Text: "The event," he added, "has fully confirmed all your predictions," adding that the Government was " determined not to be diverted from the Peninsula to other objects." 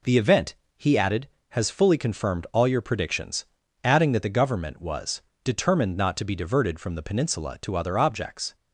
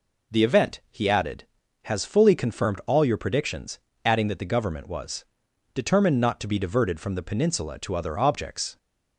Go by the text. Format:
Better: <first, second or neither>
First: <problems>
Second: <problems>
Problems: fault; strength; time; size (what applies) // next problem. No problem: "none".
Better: neither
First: none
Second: none